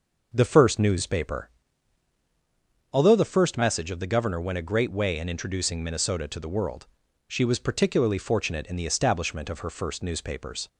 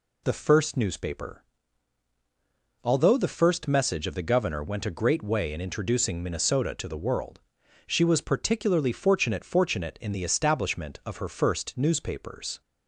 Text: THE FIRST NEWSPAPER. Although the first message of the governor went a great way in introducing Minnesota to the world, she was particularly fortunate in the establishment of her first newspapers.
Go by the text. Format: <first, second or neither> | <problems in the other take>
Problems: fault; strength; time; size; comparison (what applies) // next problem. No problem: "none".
first | says "fortunate" twice; at 9.4 s